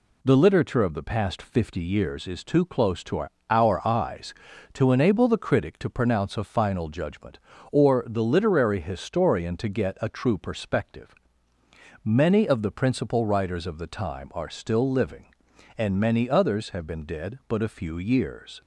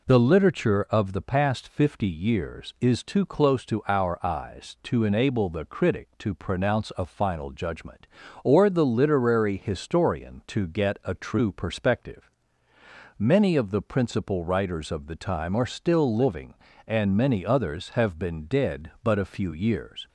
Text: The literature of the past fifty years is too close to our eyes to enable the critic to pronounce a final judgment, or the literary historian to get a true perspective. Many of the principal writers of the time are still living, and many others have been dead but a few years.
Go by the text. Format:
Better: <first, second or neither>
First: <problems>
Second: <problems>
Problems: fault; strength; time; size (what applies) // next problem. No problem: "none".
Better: second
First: says "our" twice; at 3.4 s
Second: none